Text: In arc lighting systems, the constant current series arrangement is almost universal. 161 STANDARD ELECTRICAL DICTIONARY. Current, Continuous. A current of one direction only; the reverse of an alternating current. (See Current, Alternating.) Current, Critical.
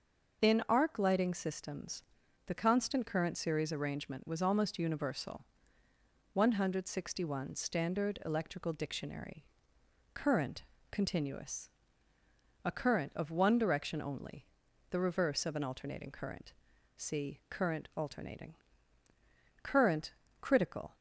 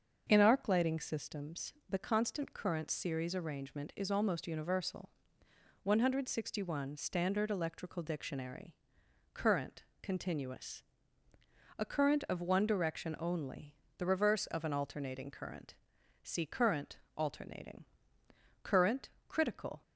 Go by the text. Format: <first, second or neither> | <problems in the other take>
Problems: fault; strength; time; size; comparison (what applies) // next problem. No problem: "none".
second | starts louder than the rest; noticeable; until 1.4 s; 6 dB; also in the second // says "was" for "is"; at 4.2 s